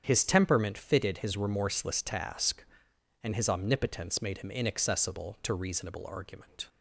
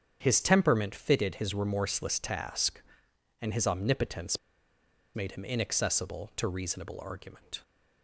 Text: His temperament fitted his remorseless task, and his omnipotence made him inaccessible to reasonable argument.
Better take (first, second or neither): first